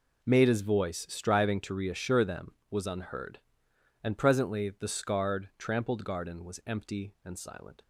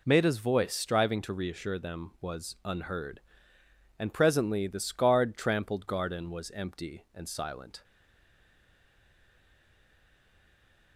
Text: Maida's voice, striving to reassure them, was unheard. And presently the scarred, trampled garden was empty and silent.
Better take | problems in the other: first | stays silent after the last word; strong; from 7.8 s on; 3.1 s long

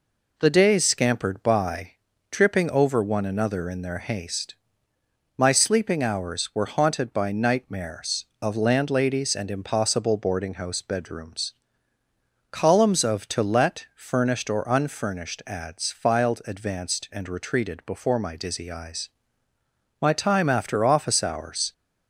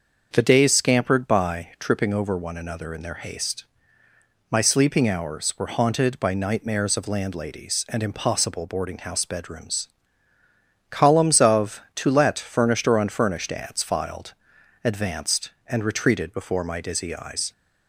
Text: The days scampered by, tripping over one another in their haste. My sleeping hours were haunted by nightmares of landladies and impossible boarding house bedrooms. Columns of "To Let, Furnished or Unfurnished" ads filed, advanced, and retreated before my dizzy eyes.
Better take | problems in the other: second | goes on to say "My time after office hours"; strong; from 20.0 s on; 1.7 s long

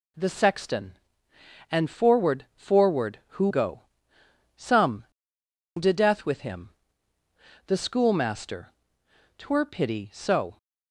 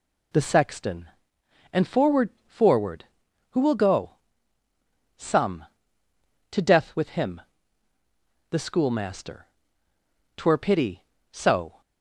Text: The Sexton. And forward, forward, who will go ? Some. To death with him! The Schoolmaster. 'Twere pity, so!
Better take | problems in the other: second | skips "will"; at 3.4 s

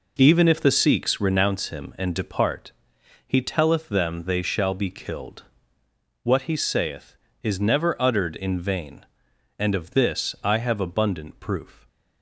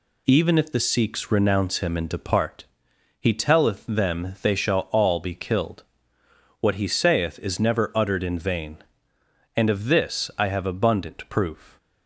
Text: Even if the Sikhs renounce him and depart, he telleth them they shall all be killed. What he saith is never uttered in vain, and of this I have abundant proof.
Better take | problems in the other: second | skips "all"; at 4.7 s

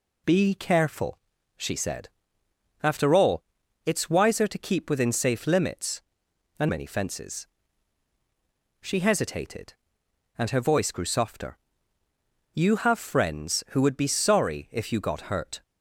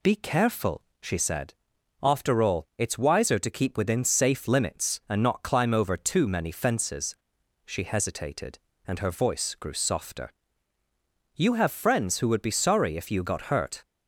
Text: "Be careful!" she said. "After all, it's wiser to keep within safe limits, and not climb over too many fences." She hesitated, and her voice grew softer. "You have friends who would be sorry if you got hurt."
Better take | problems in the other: second | skips "not climb over too"; at 6.6 s

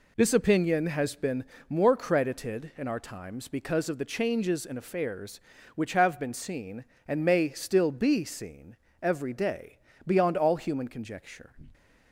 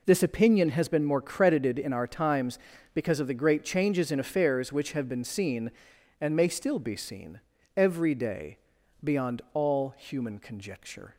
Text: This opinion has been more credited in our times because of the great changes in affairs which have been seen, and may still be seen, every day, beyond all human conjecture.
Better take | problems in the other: second | pauses between "been" and "more"; slight; at 1.4 s; 0.26 s long // skips "great"; at 4.0 s

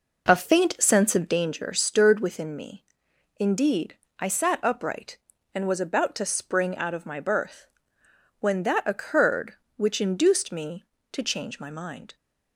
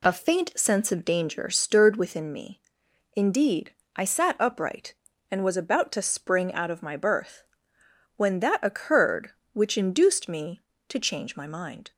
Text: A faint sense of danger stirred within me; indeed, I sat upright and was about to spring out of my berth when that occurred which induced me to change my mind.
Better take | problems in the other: second | starts louder than the rest; noticeable; until 1.4 s; 4.5 dB // pauses between "berth" and "when"; noticeable; at 7.6 s; 0.76 s long; noticeable in the second

